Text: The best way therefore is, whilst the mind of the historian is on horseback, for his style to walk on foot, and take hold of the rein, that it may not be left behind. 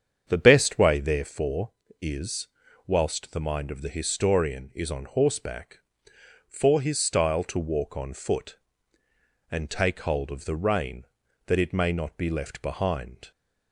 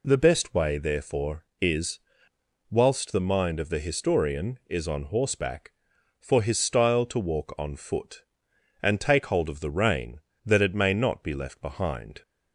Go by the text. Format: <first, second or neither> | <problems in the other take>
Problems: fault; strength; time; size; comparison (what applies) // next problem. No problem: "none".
second | starts louder than the rest; strong; until 1.4 s; 8 dB